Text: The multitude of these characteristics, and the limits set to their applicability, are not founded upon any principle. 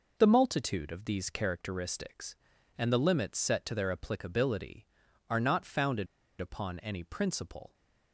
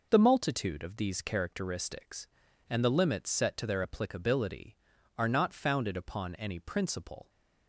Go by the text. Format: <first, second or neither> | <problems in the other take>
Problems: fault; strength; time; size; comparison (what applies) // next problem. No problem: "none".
second | pauses between "founded" and "upon"; slight; at 6.0 s; 0.32 s long